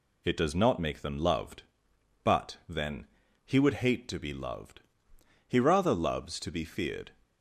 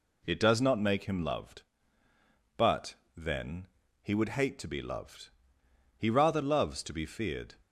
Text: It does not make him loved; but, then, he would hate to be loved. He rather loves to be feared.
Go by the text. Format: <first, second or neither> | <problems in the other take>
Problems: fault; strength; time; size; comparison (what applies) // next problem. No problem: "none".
second | says "them" for "him"; at 1.0 s